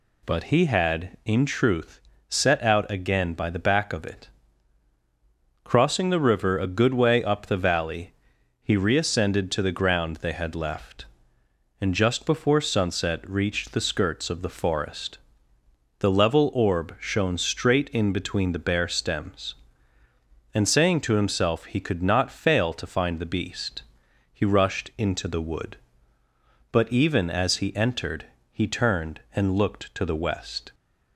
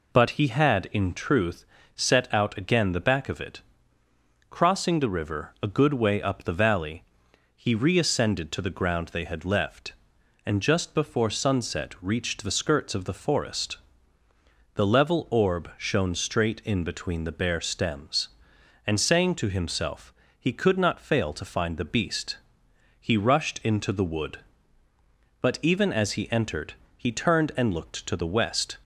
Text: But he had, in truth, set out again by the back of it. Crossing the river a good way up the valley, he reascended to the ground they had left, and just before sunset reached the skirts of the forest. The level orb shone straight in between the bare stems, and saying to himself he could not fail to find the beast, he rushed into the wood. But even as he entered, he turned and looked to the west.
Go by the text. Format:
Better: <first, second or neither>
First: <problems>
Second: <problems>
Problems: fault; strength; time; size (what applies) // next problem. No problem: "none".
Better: first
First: none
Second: skips "by"; at 2.9 s // pauses between "himself" and "he"; slight; at 20.1 s; 0.26 s long